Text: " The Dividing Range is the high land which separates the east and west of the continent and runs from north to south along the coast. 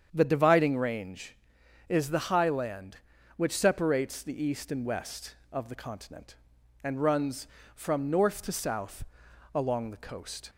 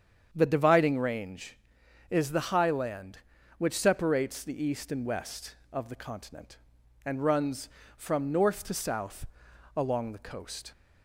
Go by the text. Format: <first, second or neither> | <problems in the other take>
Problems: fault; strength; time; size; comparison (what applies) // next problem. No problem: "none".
neither | starts louder than the rest; strong; the same in both // pauses between "south" and "along"; noticeable; the same in both